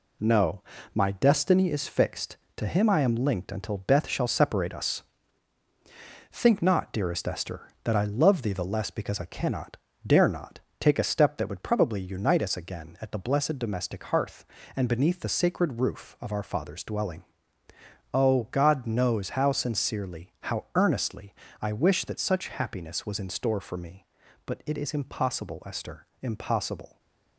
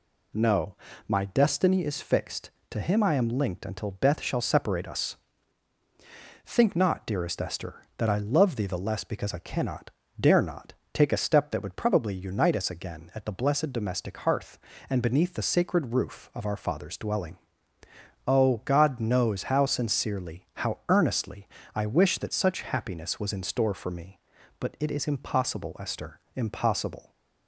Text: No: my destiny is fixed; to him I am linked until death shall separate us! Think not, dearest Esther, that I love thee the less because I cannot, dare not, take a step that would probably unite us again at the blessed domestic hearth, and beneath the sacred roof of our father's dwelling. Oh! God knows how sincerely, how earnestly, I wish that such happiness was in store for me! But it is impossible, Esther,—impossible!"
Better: second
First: gets quieter; noticeable; throughout; 5.5 dB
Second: none

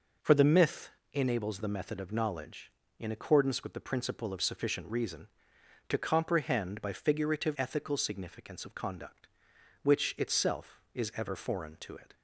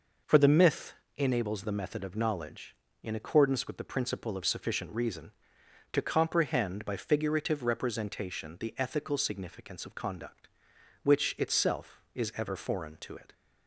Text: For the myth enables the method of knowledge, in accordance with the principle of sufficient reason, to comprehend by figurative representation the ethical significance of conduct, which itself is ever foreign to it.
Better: second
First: pauses between "myth" and "enables"; slight; at 0.9 s; 0.22 s long // skips "representation the"; at 7.5 s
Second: pauses between "myth" and "enables"; slight; at 0.9 s; 0.22 s long

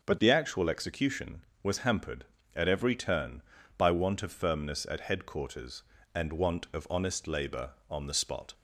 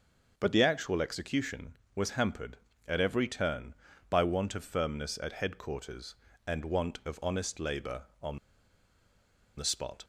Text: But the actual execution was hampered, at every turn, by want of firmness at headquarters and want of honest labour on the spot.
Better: first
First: starts louder than the rest; until 1.0 s; 6 dB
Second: starts louder than the rest; noticeable; until 1.3 s; 6 dB // pauses between "on" and "the"; at 8.3 s; 1.1 s long

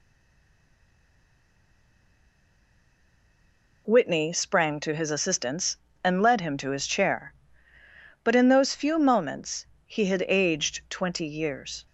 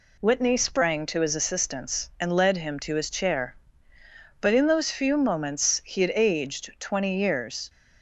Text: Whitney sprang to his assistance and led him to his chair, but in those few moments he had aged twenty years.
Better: second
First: stays silent before the first word; strong; until 3.8 s; 3.8 s long // pauses between "moments" and "he"; slight; at 9.6 s; 0.18 s long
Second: none

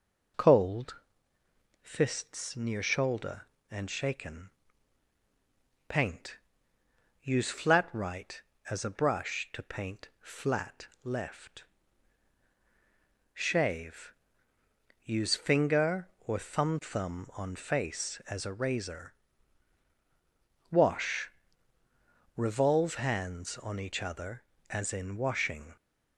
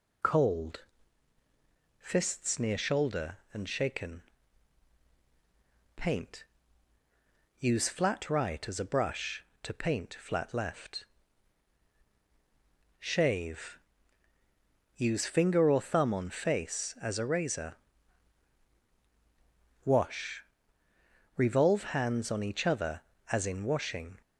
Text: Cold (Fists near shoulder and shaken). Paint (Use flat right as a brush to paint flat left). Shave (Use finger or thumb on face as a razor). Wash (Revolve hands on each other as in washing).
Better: second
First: pauses between "flat" and "left"; slight; at 10.8 s; 0.16 s long // says "thumb" twice; at 16.8 s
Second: none

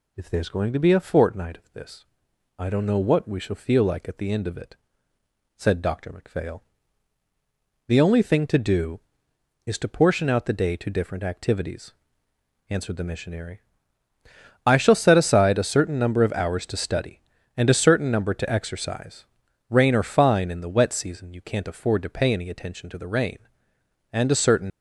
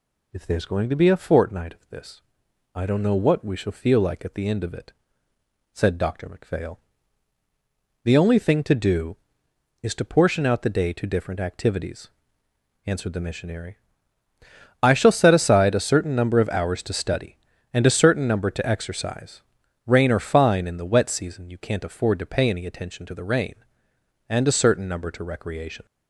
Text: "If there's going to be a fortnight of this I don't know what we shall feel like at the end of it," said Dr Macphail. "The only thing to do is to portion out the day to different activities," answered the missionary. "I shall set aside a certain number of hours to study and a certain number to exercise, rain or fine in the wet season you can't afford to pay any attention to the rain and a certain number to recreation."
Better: second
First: pauses between "this" and "I"; noticeable; at 2.0 s; 0.54 s long // stops before "number to recreation"; at 24.7 s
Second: pauses between "this" and "I"; noticeable; at 2.2 s; 0.54 s long

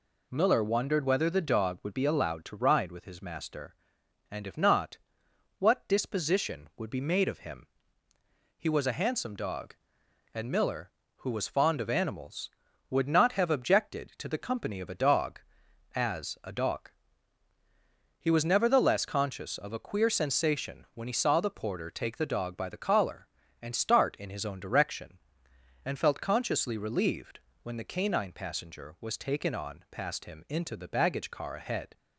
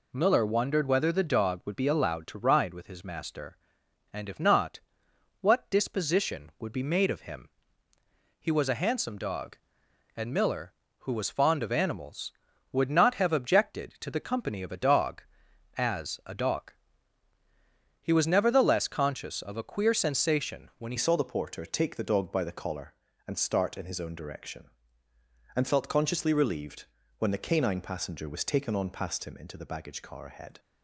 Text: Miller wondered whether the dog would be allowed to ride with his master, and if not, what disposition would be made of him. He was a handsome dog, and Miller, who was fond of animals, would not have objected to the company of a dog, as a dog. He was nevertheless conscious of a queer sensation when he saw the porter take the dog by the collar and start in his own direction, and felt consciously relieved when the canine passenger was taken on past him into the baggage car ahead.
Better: first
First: pauses between "relieved" and "when"; slight; at 27.3 s; 0.24 s long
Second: changes voice at "saw"; from 20.9 s on; 9.6 s long // pauses between "relieved" and "when"; slight; at 26.8 s; 0.34 s long

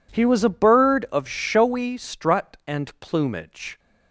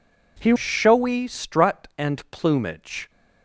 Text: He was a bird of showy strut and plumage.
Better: first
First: none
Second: skips "was a bird of"; at 0.5 s

